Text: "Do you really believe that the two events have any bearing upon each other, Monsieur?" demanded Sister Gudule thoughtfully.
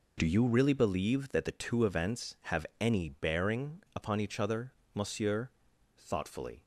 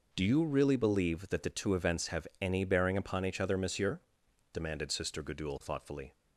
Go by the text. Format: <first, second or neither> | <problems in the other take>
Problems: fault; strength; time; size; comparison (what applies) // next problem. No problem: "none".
second | skips "demanded Sister Gudule"; at 5.7 s